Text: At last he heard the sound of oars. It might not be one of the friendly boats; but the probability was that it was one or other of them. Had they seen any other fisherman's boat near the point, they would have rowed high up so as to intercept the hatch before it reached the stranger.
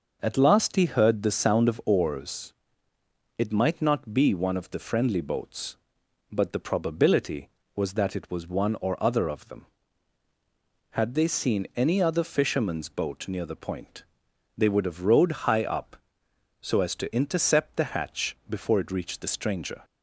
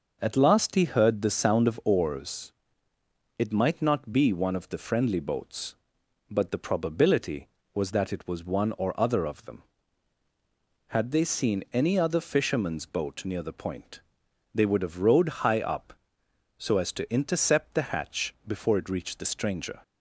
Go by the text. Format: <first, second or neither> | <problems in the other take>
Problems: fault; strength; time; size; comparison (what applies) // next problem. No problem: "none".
neither | none